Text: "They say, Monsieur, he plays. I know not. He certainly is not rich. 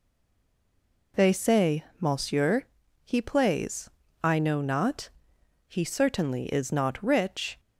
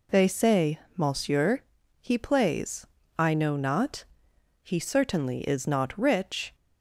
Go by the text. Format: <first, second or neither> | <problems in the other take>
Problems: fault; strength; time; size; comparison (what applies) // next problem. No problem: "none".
second | stays silent before the first word; until 1.1 s; 1.1 s long